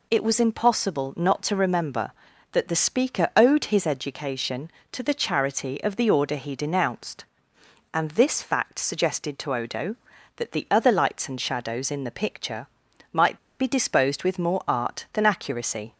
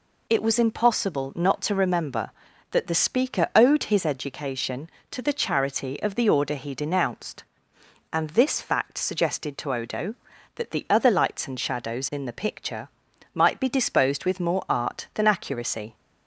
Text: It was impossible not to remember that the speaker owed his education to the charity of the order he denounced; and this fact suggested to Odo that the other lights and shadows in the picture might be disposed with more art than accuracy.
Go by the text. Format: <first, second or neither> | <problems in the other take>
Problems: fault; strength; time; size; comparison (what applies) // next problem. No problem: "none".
second | pauses between "picture" and "might"; noticeable; at 12.6 s; 0.46 s long; noticeable in the second // pauses between "might" and "be"; slight; at 13.3 s; 0.20 s long